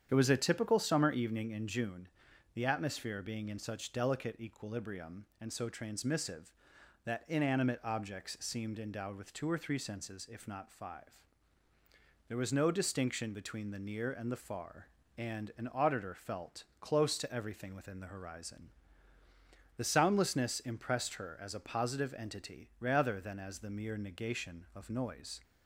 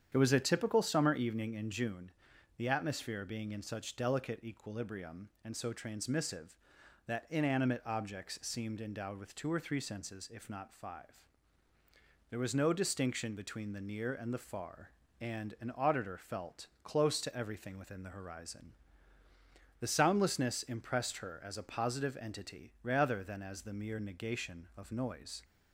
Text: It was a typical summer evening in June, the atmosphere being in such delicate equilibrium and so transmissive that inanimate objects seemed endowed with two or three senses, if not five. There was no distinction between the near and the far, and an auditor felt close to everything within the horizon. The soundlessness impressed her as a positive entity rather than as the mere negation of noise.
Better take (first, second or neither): neither